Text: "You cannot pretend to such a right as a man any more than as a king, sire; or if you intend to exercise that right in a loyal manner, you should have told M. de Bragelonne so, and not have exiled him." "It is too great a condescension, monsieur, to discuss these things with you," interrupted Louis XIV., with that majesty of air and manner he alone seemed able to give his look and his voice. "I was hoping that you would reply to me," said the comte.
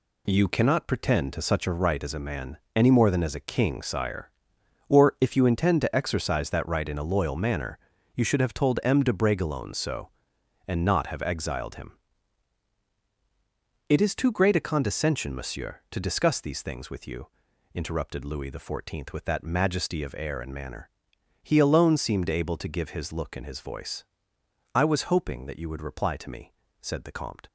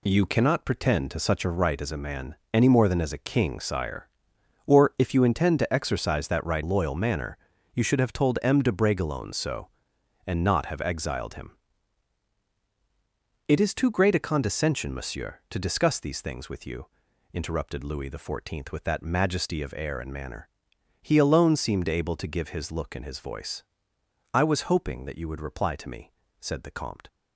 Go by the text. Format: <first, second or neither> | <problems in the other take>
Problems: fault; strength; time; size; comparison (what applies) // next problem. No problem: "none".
first | pauses between "man" and "any"; slight; at 2.3 s; 0.16 s long; slight in the first // skips "in a"; at 6.6 s // pauses between "manner" and "he"; noticeable; at 20.4 s; 0.54 s long; noticeable in the first